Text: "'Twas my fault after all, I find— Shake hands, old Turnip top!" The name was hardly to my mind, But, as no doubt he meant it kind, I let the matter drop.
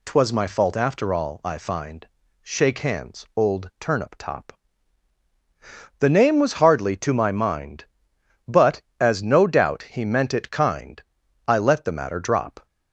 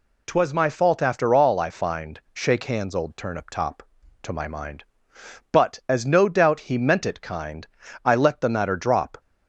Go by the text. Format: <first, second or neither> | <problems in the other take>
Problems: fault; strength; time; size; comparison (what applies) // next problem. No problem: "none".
first | skips "The name was hardly"; at 4.0 s